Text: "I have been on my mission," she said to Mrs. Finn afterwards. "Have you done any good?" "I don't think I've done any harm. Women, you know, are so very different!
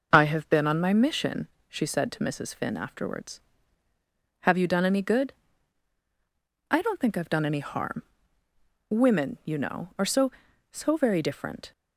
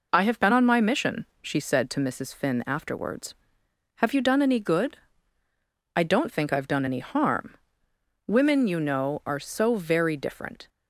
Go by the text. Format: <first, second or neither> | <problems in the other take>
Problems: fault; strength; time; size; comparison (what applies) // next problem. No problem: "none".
second | says "so" twice; at 10.7 s